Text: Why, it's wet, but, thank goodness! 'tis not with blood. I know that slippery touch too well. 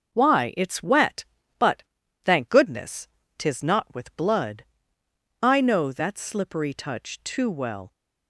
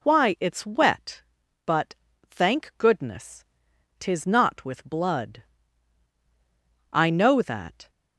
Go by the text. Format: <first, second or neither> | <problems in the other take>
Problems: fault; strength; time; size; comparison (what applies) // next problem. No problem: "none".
first | stops before "slippery touch too well"; at 7.8 s